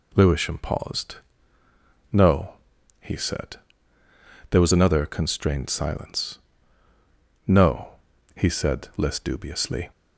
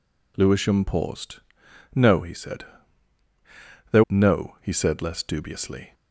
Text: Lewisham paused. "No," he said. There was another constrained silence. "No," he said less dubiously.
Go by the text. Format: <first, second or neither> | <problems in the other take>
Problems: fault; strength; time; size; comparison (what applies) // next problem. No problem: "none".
first | skips "was another constrained silence"; at 4.0 s